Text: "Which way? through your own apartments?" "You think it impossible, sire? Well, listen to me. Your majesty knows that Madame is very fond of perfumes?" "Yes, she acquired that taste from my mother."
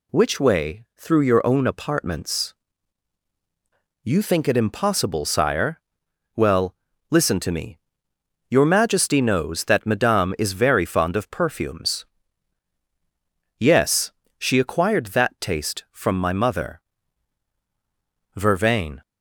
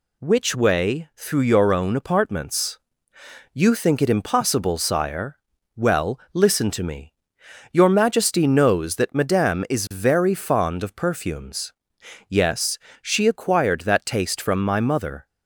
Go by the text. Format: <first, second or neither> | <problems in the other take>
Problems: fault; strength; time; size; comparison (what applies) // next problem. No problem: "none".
second | goes on to say "Vervain"; noticeable; from 18.3 s on; 0.64 s long